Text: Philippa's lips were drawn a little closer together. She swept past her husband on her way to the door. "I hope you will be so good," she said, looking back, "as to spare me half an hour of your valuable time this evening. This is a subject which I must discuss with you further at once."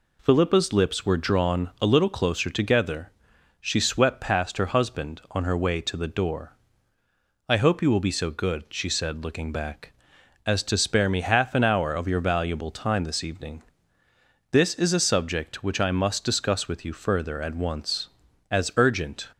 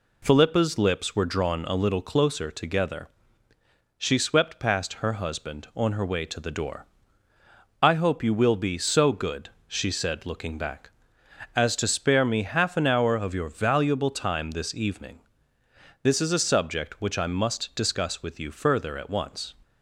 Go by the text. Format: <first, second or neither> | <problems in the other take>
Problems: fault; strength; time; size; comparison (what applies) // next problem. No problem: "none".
second | goes on to say "As urgent"; noticeable; from 18.5 s on; 0.80 s long